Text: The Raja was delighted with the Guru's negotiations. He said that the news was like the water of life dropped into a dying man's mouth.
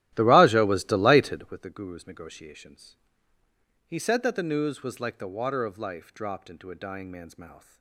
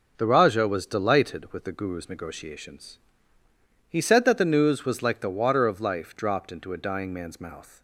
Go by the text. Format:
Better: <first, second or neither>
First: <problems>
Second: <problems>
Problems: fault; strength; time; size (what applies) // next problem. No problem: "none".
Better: second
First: starts louder than the rest; strong; until 1.6 s; 13.5 dB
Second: none